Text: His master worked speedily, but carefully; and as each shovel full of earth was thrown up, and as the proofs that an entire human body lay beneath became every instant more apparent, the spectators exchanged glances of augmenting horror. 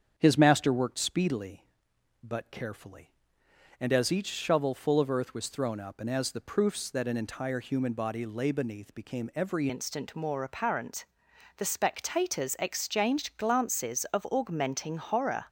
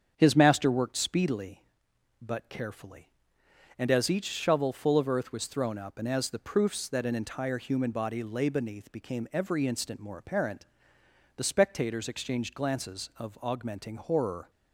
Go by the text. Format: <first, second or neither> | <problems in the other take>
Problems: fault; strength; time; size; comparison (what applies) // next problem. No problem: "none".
second | starts louder than the rest; strong; until 1.1 s; 7.5 dB; strong in the second // changes voice at "instant"; from 9.6 s on; 5.8 s long